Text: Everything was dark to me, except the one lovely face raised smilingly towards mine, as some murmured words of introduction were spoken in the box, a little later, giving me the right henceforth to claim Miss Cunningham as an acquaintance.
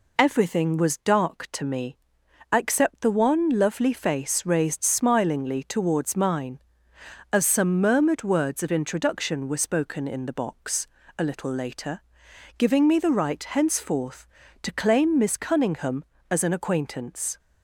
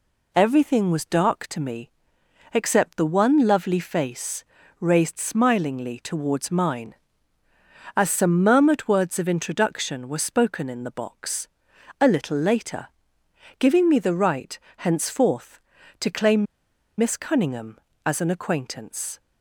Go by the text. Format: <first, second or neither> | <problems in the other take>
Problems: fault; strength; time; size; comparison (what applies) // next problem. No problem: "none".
first | pauses between "face" and "raised"; slight; at 4.4 s; 0.36 s long // pauses between "right" and "henceforth"; slight; at 14.5 s; 0.20 s long // pauses between "claim" and "Miss"; noticeable; at 16.4 s; 0.52 s long